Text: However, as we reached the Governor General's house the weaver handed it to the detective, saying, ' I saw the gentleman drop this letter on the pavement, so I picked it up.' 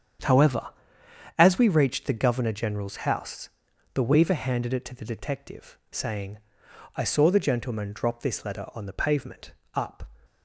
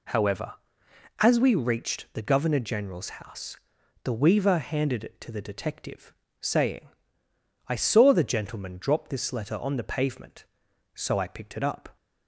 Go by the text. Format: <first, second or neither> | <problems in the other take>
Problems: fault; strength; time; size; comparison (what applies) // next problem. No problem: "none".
second | starts louder than the rest; strong; until 1.9 s; 8.5 dB // pauses between "house" and "the"; noticeable; at 3.4 s; 0.46 s long; noticeable in the second // skips "so I picked it"; at 9.6 s